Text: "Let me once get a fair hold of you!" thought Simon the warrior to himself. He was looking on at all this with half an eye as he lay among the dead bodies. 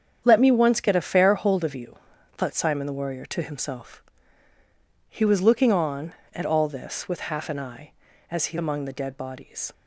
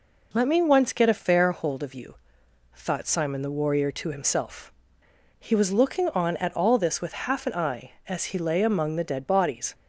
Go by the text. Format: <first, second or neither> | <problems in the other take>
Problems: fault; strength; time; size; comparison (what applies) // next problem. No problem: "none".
second | starts louder than the rest; strong; until 1.2 s; 8 dB // skips "lay"; at 8.5 s